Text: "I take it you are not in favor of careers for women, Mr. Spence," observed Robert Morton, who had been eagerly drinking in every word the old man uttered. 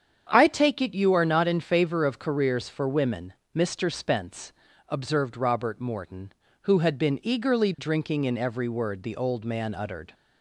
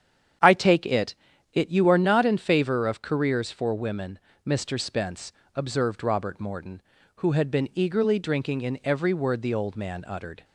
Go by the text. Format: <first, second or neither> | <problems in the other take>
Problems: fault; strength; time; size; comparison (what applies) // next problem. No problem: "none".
first | starts louder than the rest; strong; until 1.8 s; 8.5 dB; strong in the first // says "it" twice; at 1.5 s